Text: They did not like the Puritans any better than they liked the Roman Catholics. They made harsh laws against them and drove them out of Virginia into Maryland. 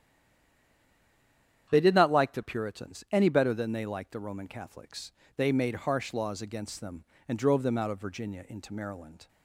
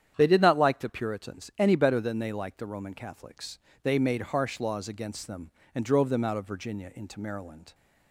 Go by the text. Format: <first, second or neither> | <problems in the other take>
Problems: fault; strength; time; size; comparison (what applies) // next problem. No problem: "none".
second | stays silent before the first word; noticeable; until 1.6 s; 1.6 s long // starts louder than the rest; strong; until 2.7 s; 9 dB; strong in the second